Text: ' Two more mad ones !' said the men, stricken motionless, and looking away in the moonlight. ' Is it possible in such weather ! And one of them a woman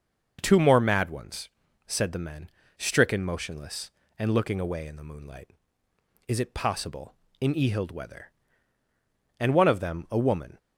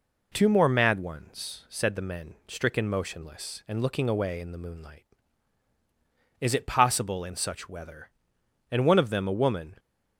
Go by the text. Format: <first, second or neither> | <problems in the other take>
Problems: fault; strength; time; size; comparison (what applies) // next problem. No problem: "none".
second | starts louder than the rest; until 1.4 s; 6.5 dB // says "ehild" for "such"; at 7.5 s